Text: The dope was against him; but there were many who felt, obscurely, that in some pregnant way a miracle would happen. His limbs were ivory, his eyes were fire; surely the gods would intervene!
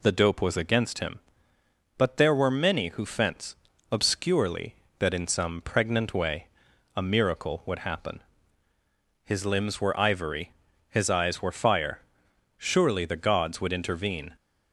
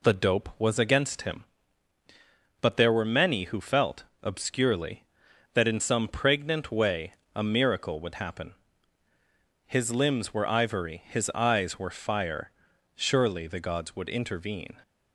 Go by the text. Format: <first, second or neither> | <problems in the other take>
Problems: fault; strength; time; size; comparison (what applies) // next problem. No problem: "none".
second | says "fence" for "felt"; at 3.0 s // pauses between "way" and "a"; noticeable; at 6.4 s; 0.48 s long; slight in the second